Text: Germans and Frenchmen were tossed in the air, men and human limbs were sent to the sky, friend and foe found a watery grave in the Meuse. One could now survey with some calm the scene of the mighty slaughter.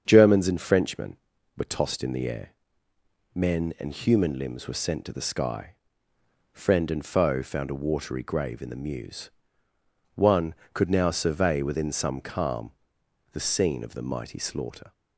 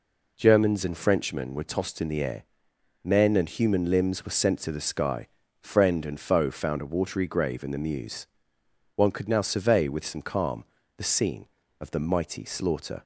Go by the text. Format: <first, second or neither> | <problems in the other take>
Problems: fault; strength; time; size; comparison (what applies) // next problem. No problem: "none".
second | starts louder than the rest; strong; until 1.0 s; 7.5 dB // says "within" for "with"; at 11.6 s // pauses between "calm" and "the"; noticeable; at 12.7 s; 0.62 s long; slight in the second